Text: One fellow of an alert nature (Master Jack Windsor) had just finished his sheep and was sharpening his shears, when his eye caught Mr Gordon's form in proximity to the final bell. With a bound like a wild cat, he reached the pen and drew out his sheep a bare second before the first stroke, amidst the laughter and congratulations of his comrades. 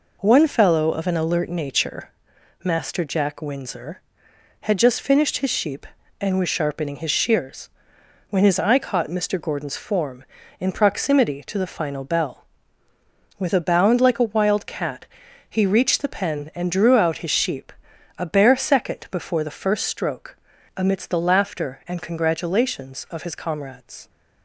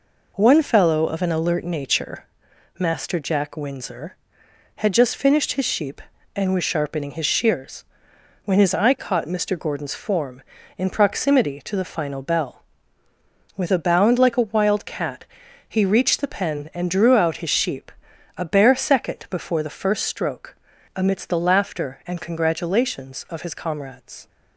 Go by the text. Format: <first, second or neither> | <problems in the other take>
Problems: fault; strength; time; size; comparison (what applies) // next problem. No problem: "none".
neither | pauses between "sheep" and "a"; noticeable; the same in both